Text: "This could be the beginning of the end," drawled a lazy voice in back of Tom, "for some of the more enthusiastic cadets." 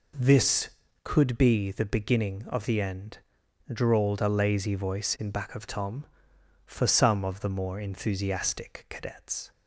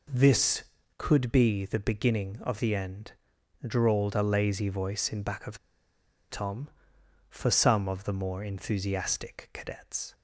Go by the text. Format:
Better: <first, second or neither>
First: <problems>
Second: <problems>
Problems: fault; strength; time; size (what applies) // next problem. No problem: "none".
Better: first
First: none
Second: pauses between "of" and "Tom"; noticeable; at 5.5 s; 0.71 s long